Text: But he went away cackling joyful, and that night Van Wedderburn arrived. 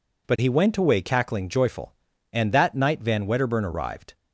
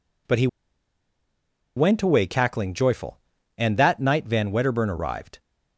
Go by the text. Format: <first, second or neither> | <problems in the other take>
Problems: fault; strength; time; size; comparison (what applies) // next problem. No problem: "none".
first | pauses between "he" and "went"; strong; at 0.4 s; 1.2 s long